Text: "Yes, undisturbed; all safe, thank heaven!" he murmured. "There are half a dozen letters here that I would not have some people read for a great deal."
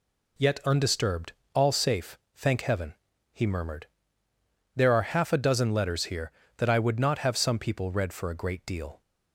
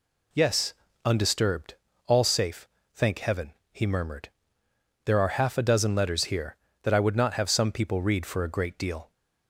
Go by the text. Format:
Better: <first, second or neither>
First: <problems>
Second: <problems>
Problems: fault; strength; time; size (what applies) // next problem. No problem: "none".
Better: second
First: says "Yet" for "Yes"; at 0.3 s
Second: none